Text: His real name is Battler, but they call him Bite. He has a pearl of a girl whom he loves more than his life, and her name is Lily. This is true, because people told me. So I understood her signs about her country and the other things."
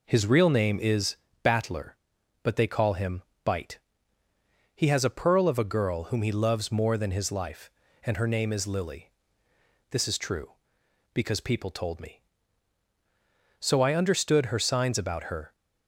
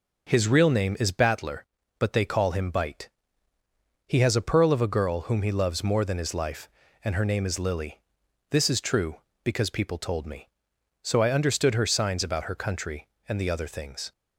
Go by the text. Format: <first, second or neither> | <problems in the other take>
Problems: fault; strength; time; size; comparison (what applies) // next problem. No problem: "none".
second | pauses between "is" and "Battler"; slight; at 1.1 s; 0.26 s long // pauses between "him" and "Bite"; slight; at 3.2 s; 0.20 s long // stops before "country and the other things"; at 15.5 s